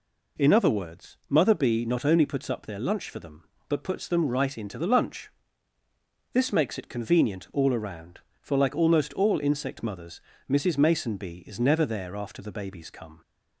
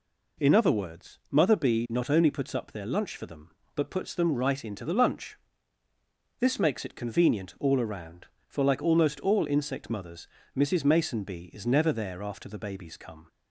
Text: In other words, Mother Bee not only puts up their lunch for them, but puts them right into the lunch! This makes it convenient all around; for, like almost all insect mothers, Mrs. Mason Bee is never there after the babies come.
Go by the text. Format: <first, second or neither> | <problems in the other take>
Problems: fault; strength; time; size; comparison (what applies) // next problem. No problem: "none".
neither | none